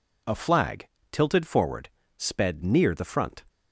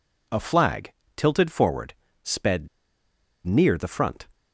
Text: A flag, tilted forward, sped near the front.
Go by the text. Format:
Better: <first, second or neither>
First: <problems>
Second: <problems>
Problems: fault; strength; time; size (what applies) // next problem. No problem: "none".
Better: first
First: none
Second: pauses between "sped" and "near"; noticeable; at 2.6 s; 0.77 s long